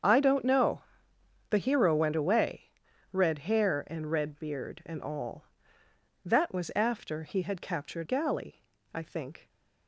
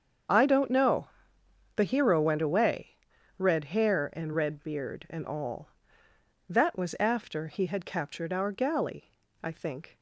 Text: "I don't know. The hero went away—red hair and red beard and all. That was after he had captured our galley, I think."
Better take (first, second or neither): second